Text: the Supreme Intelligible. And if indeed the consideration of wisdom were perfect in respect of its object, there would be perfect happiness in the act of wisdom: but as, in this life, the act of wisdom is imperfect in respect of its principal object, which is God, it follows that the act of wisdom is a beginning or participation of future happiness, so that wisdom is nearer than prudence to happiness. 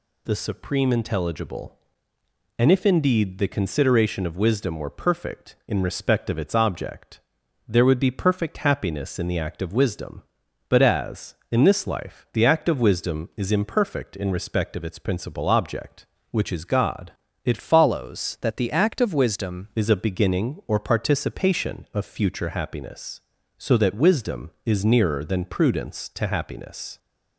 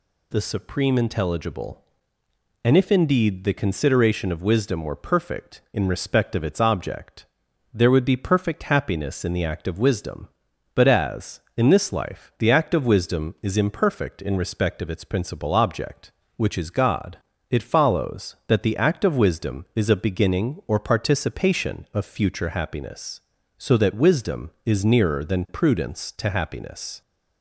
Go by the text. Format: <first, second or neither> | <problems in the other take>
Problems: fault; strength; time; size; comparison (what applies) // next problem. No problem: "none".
second | changes voice from "follows" to "wisdom"; from 17.6 to 19.6 s; 2.0 s long